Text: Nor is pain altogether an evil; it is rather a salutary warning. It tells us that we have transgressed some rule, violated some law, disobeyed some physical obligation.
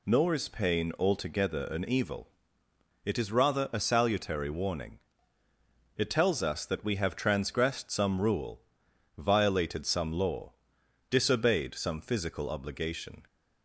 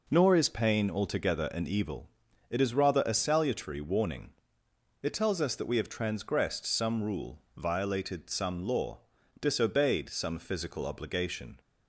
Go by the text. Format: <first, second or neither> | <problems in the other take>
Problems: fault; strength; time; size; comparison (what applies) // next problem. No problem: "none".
neither | none